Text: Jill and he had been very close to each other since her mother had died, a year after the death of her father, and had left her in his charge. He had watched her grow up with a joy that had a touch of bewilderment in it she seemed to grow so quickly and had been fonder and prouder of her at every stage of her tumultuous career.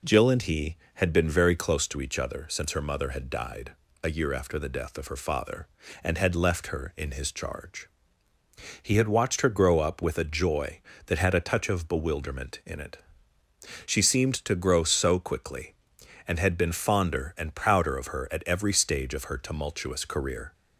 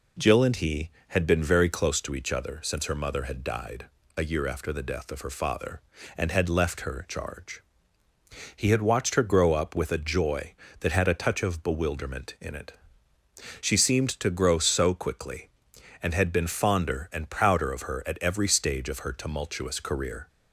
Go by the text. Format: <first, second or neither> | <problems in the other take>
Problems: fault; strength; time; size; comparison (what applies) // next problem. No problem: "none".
first | skips "in his"; at 7.0 s // pauses between "it" and "she"; noticeable; at 12.7 s; 0.88 s long; noticeable in the first